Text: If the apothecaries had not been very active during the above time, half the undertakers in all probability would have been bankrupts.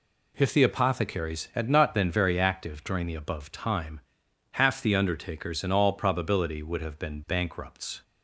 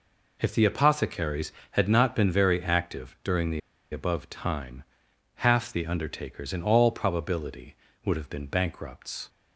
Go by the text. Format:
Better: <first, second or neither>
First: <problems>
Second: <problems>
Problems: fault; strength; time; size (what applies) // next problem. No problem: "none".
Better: first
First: none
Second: pauses between "the" and "above"; slight; at 3.6 s; 0.32 s long